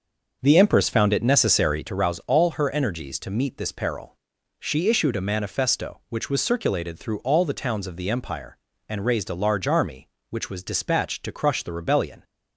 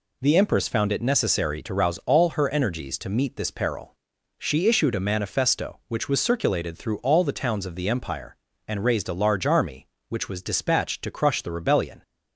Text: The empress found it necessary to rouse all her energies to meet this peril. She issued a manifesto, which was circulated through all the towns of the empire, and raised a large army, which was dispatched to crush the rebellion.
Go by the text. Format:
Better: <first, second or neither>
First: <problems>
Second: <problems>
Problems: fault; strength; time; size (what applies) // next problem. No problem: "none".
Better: second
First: starts louder than the rest; until 1.9 s; 6 dB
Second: none